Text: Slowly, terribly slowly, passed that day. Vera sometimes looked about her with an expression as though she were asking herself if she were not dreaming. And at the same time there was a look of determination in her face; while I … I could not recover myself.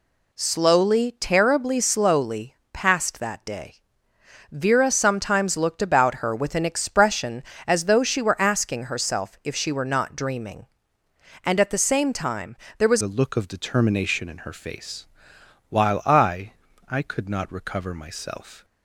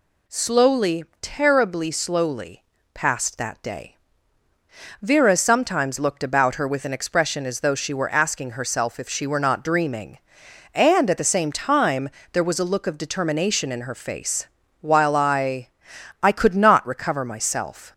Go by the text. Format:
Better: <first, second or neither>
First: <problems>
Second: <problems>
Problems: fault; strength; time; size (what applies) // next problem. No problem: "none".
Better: second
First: pauses between "time" and "there"; slight; at 12.5 s; 0.22 s long // changes voice at "a"; from 13.0 s on; 5.6 s long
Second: pauses between "time" and "there"; slight; at 12.0 s; 0.24 s long